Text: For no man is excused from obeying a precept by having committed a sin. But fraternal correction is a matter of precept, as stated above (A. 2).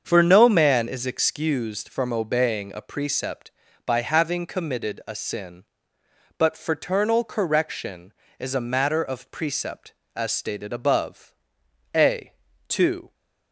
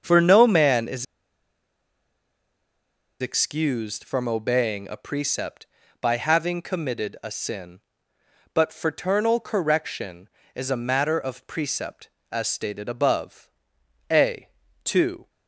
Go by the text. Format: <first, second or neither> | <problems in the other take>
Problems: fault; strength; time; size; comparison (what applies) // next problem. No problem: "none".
first | starts louder than the rest; until 1.0 s; 7 dB; also in the first // pauses between "is" and "excused"; strong; at 1.0 s; 2.1 s long